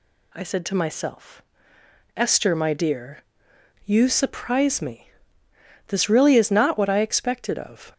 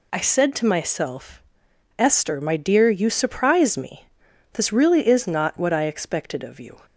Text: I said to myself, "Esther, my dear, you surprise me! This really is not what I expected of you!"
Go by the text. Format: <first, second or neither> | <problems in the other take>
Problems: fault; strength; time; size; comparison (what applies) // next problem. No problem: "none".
second | stops before "you"; at 7.9 s